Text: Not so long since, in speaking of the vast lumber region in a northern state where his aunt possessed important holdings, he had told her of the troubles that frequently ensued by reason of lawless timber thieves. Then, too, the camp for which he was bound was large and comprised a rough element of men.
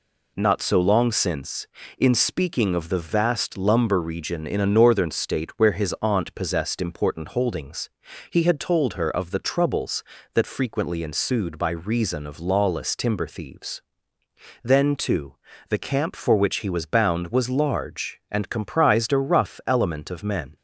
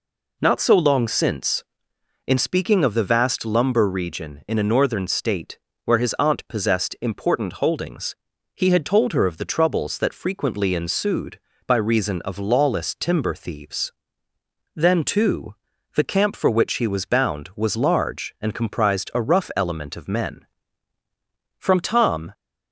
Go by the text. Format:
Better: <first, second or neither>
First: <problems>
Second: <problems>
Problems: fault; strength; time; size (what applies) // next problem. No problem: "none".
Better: first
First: none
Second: pauses between "state" and "where"; slight; at 5.5 s; 0.26 s long // goes on to say "From Tom"; noticeable; from 21.5 s on; 0.74 s long